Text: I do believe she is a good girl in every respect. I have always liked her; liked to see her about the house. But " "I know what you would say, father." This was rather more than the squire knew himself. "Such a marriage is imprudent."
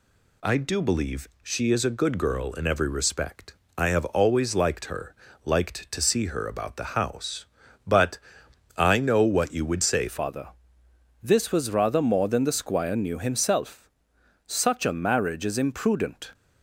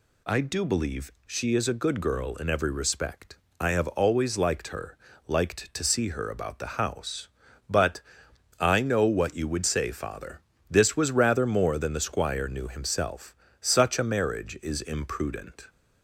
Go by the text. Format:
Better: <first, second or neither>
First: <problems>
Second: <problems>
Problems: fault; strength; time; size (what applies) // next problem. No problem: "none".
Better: second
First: changes voice at "father"; from 10.0 s on; 6.3 s long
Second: none